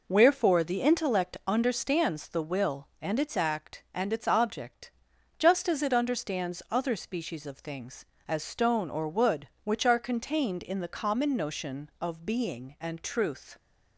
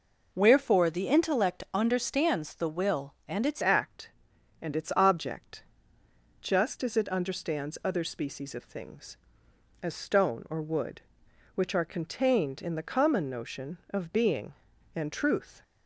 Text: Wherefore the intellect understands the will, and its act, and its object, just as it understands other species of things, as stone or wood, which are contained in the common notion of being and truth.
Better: first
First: none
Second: changes voice at "act"; from 3.6 s on; 12.0 s long

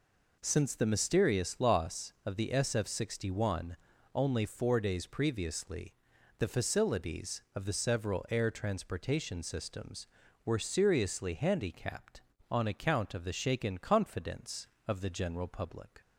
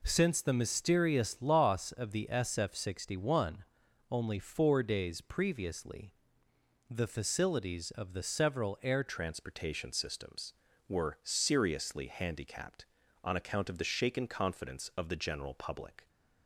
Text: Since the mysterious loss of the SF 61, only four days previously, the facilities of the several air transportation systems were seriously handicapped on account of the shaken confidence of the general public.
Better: first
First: none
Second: changes voice at "transportation"; from 9.0 s on; 7.0 s long

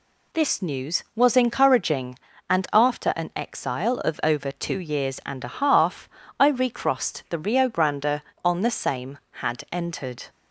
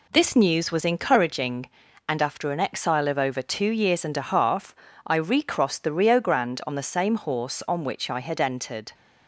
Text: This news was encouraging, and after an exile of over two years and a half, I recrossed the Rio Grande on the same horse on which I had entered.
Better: second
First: skips "horse on which I"; at 9.2 s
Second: none

